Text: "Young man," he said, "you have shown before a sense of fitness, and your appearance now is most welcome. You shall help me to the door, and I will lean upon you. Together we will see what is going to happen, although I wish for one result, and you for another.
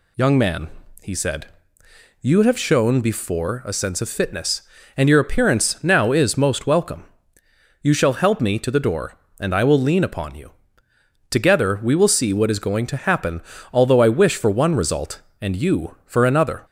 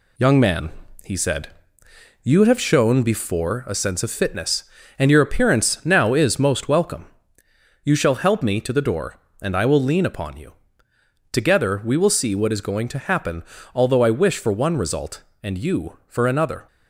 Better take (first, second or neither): first